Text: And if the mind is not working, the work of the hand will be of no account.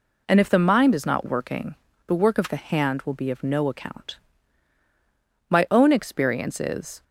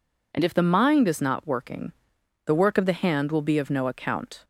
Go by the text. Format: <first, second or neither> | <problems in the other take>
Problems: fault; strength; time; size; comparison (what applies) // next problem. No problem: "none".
second | goes on to say "My own experience is"; from 5.4 s on; 1.5 s long